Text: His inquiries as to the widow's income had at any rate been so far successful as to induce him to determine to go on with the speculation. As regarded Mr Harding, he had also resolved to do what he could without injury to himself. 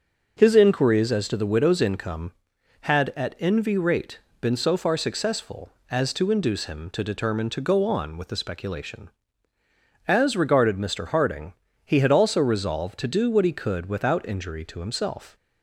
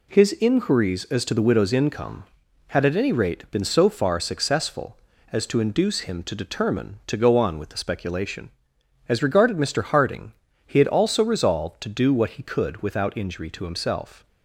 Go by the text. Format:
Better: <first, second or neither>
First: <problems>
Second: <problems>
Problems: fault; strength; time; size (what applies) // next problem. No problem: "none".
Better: second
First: starts louder than the rest; until 1.4 s; 6.5 dB // says "envy" for "any"; at 3.3 s // pauses between "rate" and "been"; slight; at 4.1 s; 0.20 s long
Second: none